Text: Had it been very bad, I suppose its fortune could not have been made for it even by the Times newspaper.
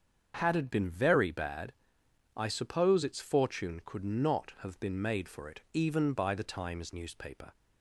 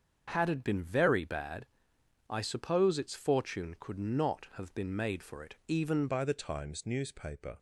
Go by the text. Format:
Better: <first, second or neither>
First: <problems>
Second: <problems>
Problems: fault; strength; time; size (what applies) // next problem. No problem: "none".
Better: first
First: starts louder than the rest; until 1.4 s; 7 dB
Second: starts louder than the rest; until 1.3 s; 6.5 dB // changes voice at "by"; from 6.0 s on; 1.5 s long